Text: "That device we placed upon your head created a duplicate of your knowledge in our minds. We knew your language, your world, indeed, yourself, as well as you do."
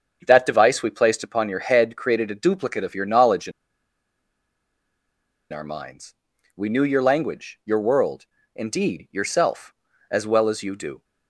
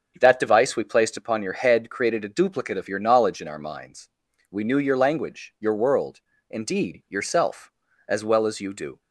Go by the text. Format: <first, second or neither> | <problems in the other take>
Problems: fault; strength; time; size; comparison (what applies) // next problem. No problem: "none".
second | starts louder than the rest; strong; until 1.2 s; 7.5 dB; strong in the second // pauses between "in" and "our"; strong; at 3.5 s; 2.0 s long